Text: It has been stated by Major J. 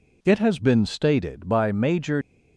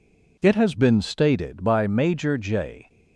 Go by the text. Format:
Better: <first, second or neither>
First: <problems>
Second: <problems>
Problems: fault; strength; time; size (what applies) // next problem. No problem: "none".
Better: second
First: stops before "J"; at 2.2 s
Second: none